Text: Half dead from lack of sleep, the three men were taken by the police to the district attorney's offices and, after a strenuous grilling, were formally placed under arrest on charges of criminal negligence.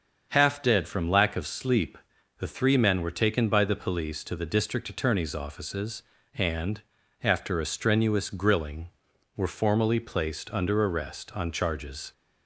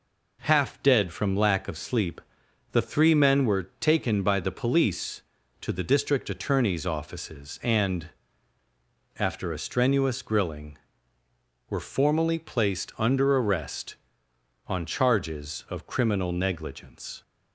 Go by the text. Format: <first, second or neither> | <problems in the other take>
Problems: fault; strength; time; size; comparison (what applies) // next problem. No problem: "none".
second | starts louder than the rest; until 1.3 s; 6.5 dB // stops before "of criminal negligence"; at 12.1 s